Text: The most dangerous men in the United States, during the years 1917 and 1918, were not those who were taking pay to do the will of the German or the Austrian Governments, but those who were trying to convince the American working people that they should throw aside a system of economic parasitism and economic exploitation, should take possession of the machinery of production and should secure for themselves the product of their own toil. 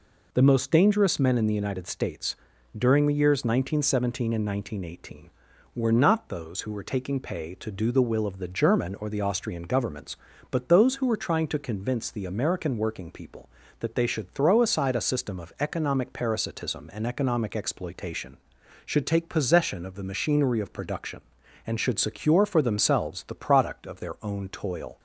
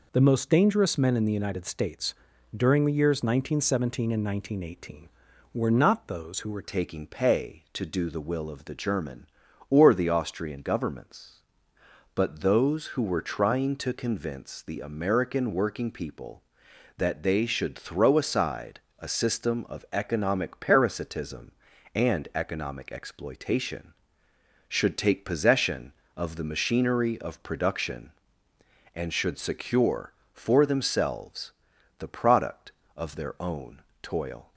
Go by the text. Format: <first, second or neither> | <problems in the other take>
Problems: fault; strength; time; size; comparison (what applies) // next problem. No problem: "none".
first | changes voice at "taking"; from 6.6 s on; 27.9 s long // pauses between "aside" and "a"; slight; at 18.7 s; 0.22 s long // pauses between "themselves" and "the"; noticeable; at 31.4 s; 0.48 s long // pauses between "own" and "toil"; slight; at 33.7 s; 0.24 s long